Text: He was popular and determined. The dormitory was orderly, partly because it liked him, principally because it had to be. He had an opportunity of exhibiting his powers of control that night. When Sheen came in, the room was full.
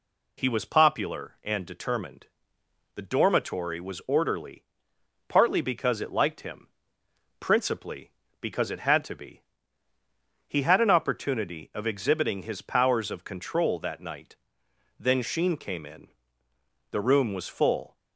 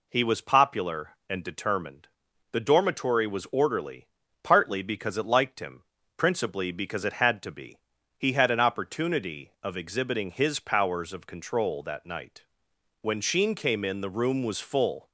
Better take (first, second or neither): second